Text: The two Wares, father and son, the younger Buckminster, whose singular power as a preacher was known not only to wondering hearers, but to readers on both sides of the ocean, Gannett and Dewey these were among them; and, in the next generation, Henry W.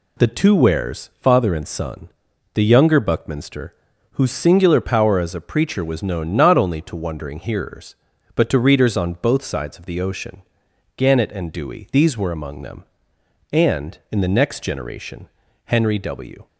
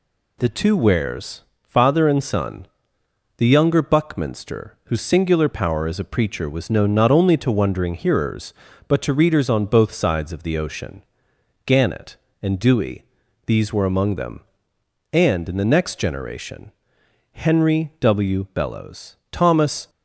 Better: first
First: none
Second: pauses between "Dewey" and "these"; at 13.0 s; 0.44 s long // goes on to say "Bellows Thomas"; from 18.5 s on; 1.3 s long

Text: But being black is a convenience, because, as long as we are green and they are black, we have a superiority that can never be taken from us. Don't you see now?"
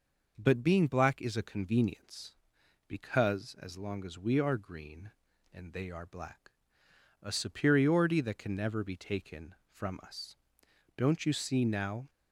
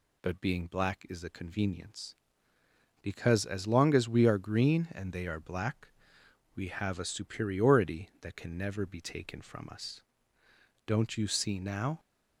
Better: second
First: skips "we have"; at 6.8 s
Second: none

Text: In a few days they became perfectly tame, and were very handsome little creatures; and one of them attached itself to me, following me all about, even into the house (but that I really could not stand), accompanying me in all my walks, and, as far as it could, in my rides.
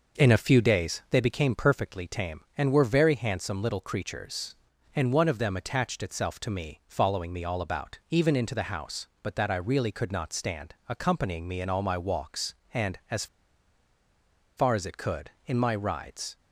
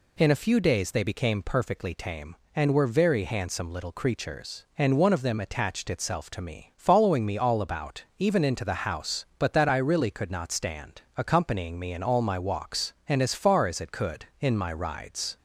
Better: second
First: pauses between "as" and "far"; strong; at 13.2 s; 1.3 s long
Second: none

